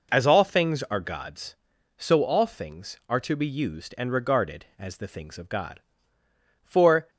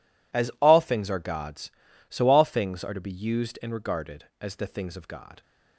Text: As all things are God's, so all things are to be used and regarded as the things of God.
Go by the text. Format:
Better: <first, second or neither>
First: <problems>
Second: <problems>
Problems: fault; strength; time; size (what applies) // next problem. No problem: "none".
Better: second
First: goes on to say "For"; slight; from 6.6 s on; 0.46 s long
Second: none